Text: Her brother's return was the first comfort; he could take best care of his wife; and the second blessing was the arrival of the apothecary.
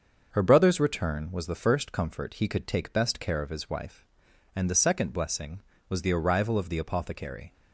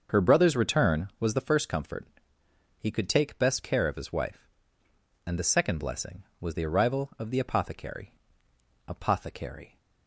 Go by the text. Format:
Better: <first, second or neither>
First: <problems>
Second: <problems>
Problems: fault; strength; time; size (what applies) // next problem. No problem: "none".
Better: first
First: starts louder than the rest; until 1.3 s; 6.5 dB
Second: starts louder than the rest; until 1.2 s; 6.5 dB // says "apothecary" twice; at 8.8 s